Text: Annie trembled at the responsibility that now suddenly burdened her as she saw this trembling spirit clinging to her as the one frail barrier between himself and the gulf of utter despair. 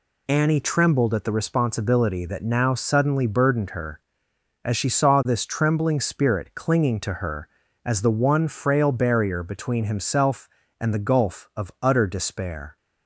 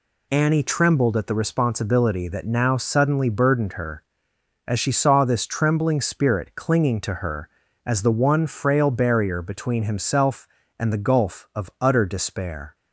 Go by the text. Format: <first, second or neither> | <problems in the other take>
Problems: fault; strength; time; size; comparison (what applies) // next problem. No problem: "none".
neither | none